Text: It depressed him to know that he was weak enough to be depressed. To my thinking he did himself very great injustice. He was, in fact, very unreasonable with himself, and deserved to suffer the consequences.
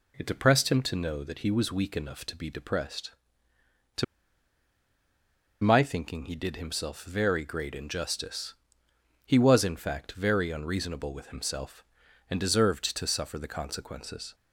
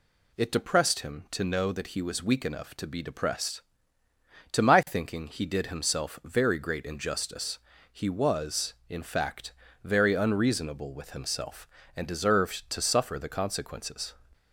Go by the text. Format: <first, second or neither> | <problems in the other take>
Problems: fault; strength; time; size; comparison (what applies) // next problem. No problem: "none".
second | pauses between "To" and "my"; strong; at 4.0 s; 1.5 s long